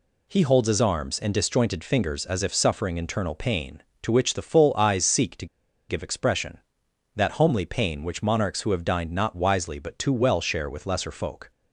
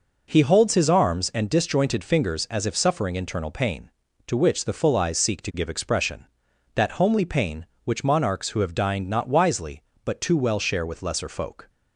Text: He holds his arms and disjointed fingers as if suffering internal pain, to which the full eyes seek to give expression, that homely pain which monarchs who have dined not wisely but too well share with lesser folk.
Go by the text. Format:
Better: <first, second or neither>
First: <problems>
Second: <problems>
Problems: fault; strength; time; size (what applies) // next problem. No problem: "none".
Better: second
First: pauses between "to" and "give"; at 5.4 s; 0.43 s long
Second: none